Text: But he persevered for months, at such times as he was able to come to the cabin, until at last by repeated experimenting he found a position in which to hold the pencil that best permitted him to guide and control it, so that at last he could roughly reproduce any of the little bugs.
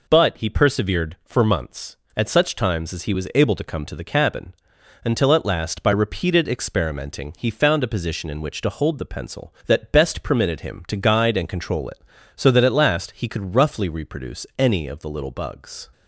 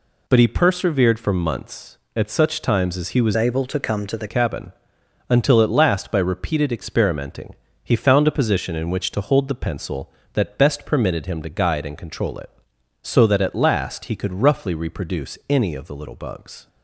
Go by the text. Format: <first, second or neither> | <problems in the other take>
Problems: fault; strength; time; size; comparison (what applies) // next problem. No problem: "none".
first | changes voice from "able" to "the"; from 3.3 to 4.2 s; 0.9 s long // pauses between "experimenting" and "he"; slight; at 7.5 s; 0.30 s long